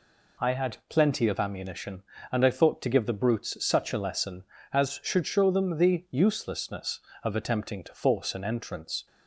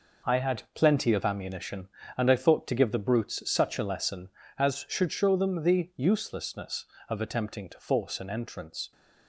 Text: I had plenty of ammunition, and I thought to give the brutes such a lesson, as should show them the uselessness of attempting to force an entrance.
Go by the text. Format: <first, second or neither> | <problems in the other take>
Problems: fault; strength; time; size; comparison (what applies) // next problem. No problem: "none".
first | gets quieter; strong; throughout; 8 dB